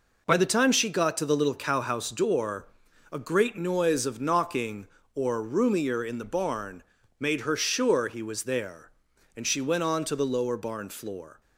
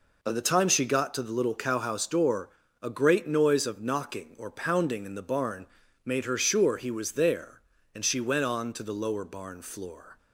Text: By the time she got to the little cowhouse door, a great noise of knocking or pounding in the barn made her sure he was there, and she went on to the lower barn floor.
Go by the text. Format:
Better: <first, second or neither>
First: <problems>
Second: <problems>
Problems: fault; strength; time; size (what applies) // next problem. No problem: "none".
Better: second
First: says "roomier" for "pounding"; at 5.4 s // pauses between "barn" and "made"; at 6.8 s; 0.38 s long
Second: pauses between "barn" and "made"; at 5.6 s; 0.40 s long